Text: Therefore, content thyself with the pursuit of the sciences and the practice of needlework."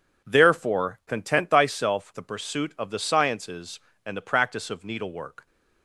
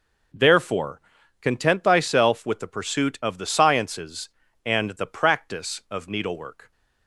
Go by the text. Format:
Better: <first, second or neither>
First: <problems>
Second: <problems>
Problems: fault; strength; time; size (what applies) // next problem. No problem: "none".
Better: second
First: skips "with"; at 2.1 s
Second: none